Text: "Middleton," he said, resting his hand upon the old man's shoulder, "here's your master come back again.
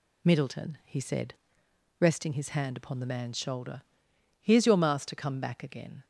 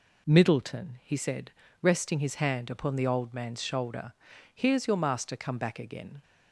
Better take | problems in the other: second | skips "old"; at 3.0 s

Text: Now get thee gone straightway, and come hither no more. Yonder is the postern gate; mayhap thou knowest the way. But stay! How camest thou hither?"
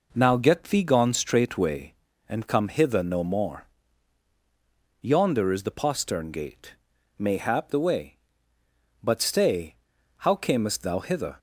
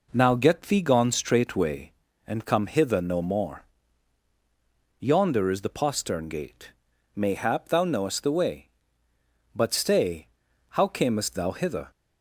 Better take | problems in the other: second | skips "thou knowest"; at 7.7 s

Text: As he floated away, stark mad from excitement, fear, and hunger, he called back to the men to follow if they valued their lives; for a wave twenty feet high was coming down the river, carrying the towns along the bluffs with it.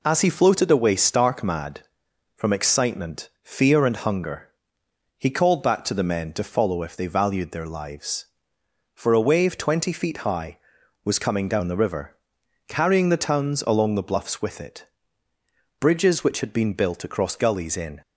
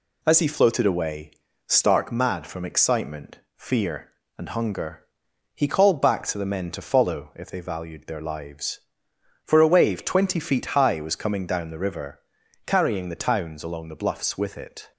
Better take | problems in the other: second | goes on to say "Bridges which had been built across gullies in"; strong; from 15.7 s on; 2.2 s long

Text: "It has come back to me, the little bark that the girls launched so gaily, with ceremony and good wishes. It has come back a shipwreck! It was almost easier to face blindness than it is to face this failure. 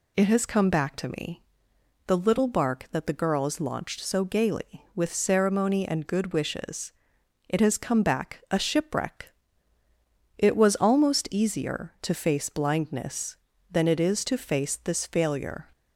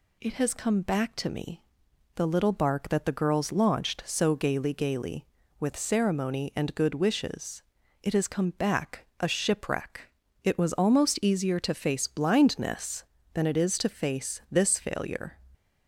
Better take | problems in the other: first | says "gaily" twice; at 4.7 s

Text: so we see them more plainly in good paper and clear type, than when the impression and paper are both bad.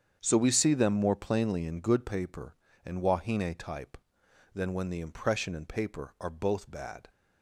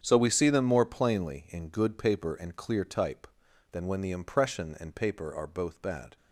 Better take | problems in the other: second | starts louder than the rest; strong; until 1.2 s; 8 dB; strong in the second // says "wahine" for "clear"; at 3.0 s

